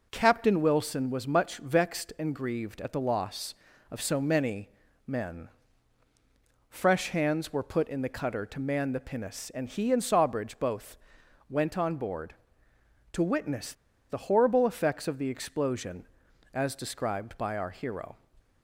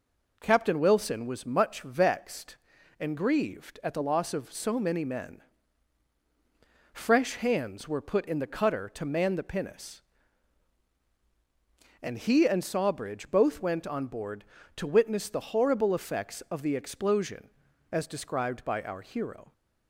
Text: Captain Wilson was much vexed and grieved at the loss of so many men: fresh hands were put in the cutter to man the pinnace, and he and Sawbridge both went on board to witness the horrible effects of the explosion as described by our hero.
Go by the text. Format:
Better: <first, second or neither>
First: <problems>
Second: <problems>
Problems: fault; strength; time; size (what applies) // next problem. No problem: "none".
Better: second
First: pauses between "many" and "men"; slight; at 4.6 s; 0.36 s long // pauses between "both" and "went"; noticeable; at 10.9 s; 0.52 s long // pauses between "witness" and "the"; at 13.7 s; 0.36 s long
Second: none